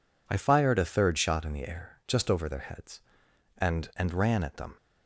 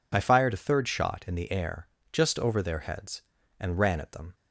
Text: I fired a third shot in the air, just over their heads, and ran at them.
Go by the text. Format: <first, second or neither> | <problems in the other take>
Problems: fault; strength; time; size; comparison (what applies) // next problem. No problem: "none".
second | says "and" twice; at 3.9 s